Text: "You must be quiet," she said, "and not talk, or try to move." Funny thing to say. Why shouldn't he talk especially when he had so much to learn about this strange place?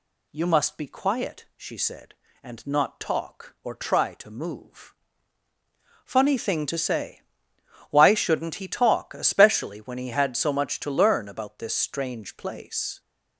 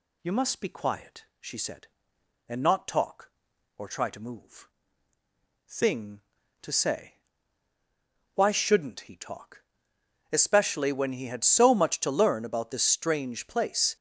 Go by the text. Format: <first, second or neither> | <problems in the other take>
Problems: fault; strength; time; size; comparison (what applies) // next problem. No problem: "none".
first | skips "Funny"; at 5.1 s // pauses between "talk" and "especially"; noticeable; at 9.6 s; 0.66 s long